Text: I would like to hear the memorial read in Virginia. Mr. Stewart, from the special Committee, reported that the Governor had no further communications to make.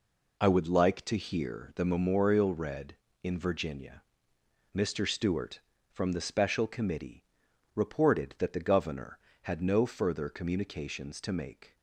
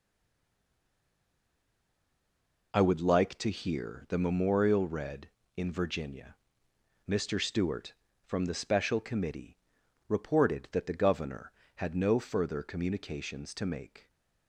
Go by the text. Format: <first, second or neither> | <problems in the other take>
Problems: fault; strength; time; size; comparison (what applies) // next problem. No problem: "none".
first | stays silent before the first word; strong; until 2.7 s; 2.7 s long